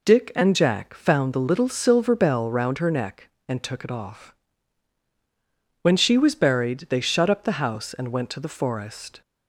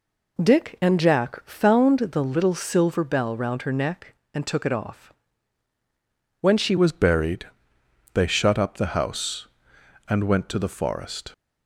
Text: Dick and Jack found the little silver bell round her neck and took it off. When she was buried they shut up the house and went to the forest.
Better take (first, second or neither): first